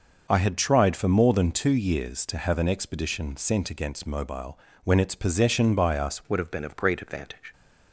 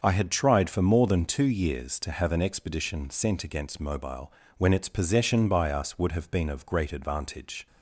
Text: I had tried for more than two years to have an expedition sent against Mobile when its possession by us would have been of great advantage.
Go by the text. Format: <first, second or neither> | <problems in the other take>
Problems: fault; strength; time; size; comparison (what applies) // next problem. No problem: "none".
second | starts louder than the rest; noticeable; until 1.3 s; 6 dB; also in the second // pauses between "Mobile" and "when"; slight; at 4.5 s; 0.28 s long; slight in the second // changes voice at "would"; from 6.2 s on; 1.3 s long